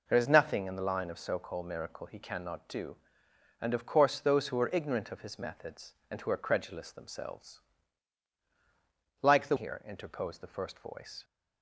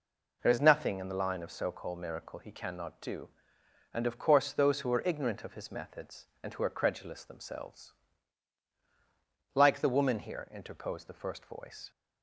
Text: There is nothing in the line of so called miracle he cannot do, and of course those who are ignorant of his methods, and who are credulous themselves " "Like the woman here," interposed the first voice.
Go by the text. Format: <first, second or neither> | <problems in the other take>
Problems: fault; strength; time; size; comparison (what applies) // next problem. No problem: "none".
second | skips "woman"; at 9.5 s